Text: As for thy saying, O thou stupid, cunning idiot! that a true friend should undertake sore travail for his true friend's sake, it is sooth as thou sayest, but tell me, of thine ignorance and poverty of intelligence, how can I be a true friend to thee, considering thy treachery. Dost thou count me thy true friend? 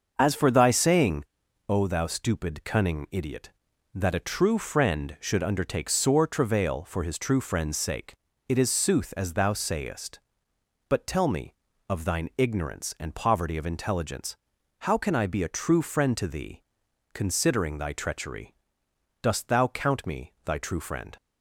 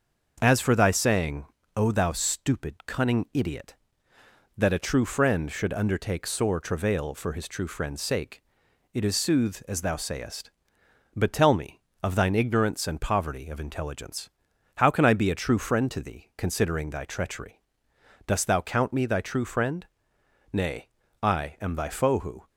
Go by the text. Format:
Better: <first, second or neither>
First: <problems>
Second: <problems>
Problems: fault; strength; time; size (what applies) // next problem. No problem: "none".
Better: first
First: starts louder than the rest; until 1.1 s; 6 dB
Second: starts louder than the rest; until 1.4 s; 6 dB // goes on to say "Nay I am thy foe who"; strong; from 20.5 s on; 1.9 s long